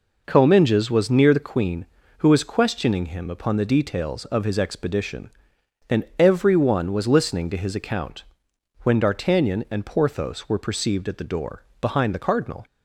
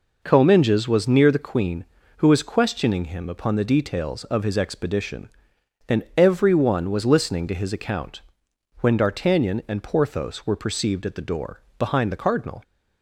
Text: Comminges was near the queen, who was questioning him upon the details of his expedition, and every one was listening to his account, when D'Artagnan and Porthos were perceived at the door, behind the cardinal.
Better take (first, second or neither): neither